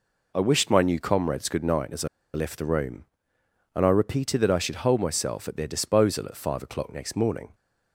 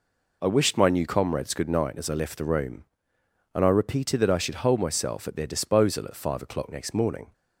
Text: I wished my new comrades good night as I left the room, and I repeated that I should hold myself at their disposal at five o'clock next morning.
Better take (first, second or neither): second